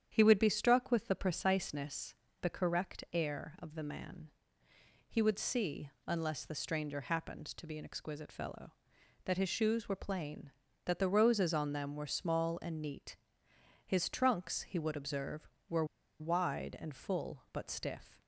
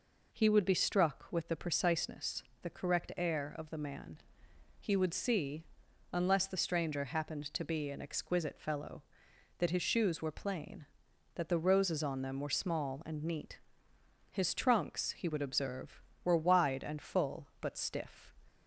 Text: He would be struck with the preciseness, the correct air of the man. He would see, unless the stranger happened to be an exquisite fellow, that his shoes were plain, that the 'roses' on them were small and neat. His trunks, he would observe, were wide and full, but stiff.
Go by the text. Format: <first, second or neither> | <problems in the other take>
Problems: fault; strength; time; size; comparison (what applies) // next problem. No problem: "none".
second | starts louder than the rest; strong; until 1.1 s; 9 dB // pauses between "were" and "wide"; slight; at 15.8 s; 0.35 s long